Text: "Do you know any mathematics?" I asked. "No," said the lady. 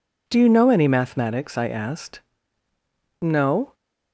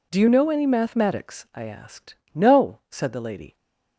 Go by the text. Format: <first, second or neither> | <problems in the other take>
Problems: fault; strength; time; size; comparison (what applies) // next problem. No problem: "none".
second | stops before "said the lady"; at 3.7 s